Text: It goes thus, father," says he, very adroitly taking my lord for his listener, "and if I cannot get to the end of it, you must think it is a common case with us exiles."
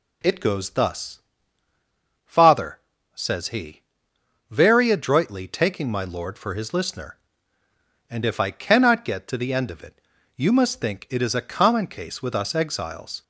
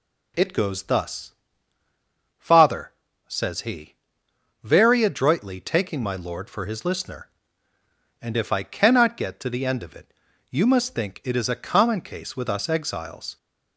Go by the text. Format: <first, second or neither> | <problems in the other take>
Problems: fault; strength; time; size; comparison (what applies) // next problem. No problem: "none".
neither | none